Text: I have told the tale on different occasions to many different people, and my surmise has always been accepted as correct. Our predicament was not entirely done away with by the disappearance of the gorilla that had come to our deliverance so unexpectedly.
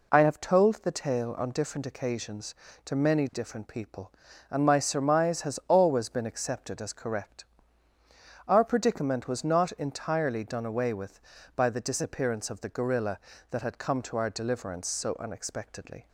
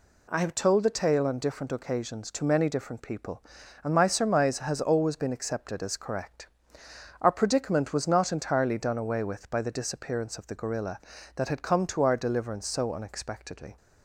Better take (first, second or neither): neither